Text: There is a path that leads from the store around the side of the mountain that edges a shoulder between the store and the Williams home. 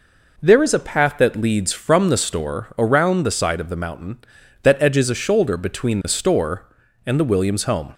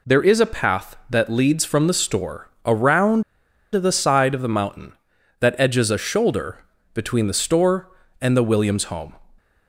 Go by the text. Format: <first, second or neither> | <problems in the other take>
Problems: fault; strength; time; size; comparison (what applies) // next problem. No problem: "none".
first | pauses between "store" and "around"; slight; at 2.4 s; 0.16 s long // pauses between "around" and "the"; noticeable; at 3.2 s; 0.50 s long // pauses between "shoulder" and "between"; slight; at 6.5 s; 0.36 s long